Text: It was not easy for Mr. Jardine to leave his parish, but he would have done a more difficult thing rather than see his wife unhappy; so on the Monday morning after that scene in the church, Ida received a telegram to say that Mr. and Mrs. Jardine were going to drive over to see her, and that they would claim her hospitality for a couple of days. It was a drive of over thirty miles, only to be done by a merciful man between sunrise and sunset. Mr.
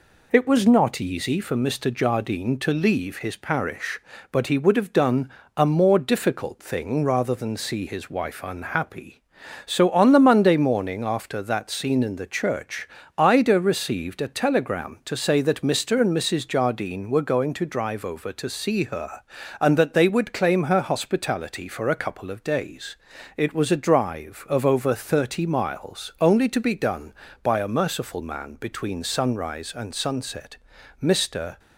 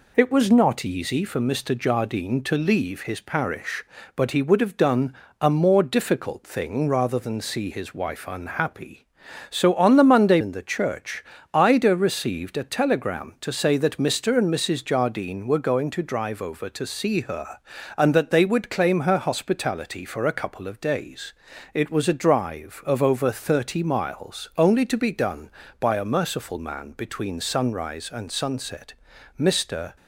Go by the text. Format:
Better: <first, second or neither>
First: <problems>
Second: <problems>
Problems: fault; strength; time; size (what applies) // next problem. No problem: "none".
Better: first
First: pauses between "done" and "a"; slight; at 5.2 s; 0.26 s long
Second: pauses between "done" and "a"; slight; at 5.1 s; 0.26 s long // skips "morning after that scene"; at 10.4 s